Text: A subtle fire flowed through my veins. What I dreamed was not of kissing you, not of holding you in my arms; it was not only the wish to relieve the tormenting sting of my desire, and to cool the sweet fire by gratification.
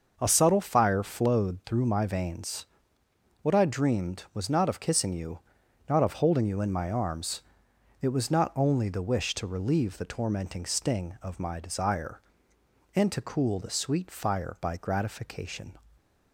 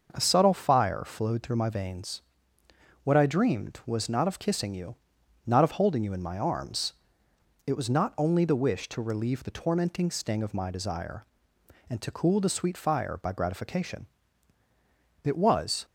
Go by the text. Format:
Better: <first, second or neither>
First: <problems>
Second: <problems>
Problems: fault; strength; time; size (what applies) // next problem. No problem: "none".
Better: first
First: starts louder than the rest; until 1.2 s; 6 dB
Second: starts louder than the rest; until 1.1 s; 6.5 dB // goes on to say "It was"; noticeable; from 15.2 s on; 0.62 s long